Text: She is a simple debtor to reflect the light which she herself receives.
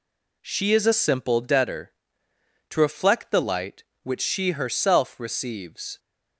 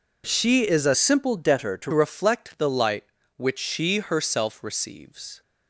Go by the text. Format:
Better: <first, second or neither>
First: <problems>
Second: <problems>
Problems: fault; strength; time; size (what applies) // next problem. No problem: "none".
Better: first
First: none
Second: changes voice from "simple" to "to"; from 0.9 to 1.9 s; 1.0 s long